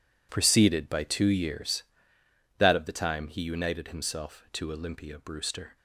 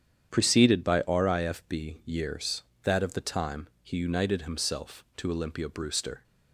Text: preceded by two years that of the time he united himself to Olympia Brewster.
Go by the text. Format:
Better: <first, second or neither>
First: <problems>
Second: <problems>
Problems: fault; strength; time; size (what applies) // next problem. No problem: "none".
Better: first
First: none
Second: starts louder than the rest; strong; until 1.3 s; 9 dB // says "rifb" for "two"; at 1.0 s